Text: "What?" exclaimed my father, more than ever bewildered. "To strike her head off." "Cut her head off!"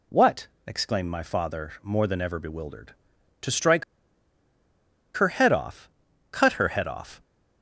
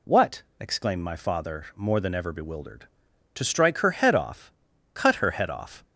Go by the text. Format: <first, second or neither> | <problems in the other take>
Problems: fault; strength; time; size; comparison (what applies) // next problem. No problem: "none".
second | pauses between "strike" and "her"; strong; at 3.8 s; 1.3 s long